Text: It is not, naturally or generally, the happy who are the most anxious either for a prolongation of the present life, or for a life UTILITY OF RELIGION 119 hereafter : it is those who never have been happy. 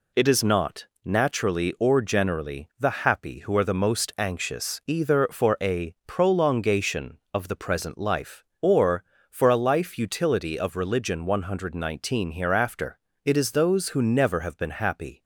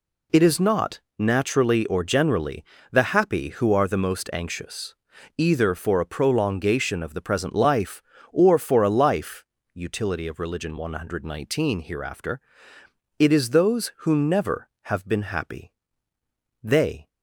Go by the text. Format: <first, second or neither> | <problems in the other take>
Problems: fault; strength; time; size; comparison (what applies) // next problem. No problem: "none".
first | pauses between "anxious" and "either"; at 4.9 s; 0.42 s long // pauses between "life" and "UTILITY"; slight; at 9.4 s; 0.30 s long // goes on to say "They"; slight; from 16.6 s on; 0.44 s long